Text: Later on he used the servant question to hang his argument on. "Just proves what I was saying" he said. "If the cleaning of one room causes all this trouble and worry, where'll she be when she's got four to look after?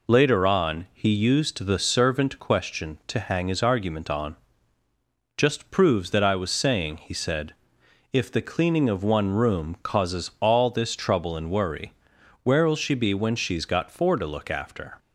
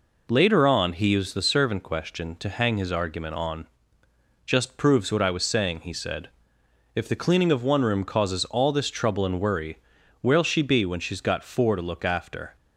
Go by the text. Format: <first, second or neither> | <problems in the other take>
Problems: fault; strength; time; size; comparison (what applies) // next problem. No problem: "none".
second | says "that" for "what"; at 6.1 s